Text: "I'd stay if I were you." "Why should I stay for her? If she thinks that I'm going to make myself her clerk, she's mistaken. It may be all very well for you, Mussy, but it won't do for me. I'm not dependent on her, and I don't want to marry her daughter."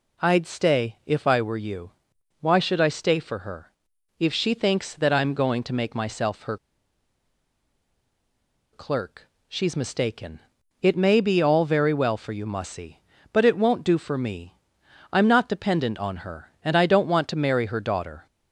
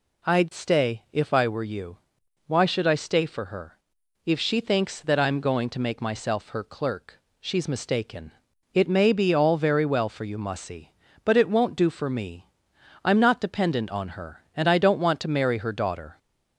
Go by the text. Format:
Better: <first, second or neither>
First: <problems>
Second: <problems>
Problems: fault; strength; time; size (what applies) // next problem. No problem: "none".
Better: second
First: pauses between "her" and "clerk"; strong; at 6.5 s; 2.1 s long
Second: none